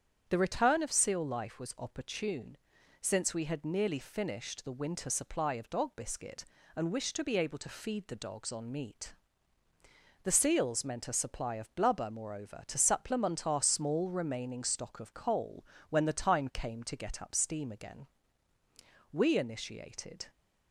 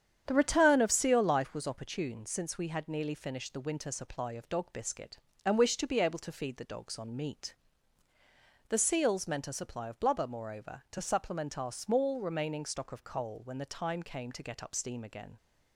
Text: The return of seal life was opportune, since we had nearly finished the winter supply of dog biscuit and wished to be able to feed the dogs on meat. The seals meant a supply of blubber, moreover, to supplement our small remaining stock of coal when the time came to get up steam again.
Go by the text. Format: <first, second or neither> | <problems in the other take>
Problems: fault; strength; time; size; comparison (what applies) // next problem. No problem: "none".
second | starts louder than the rest; strong; until 1.2 s; 8.5 dB; strong in the second // pauses between "coal" and "when"; slight; at 15.6 s; 0.26 s long // goes on to say "We initiated"; noticeable; from 19.1 s on; 1.1 s long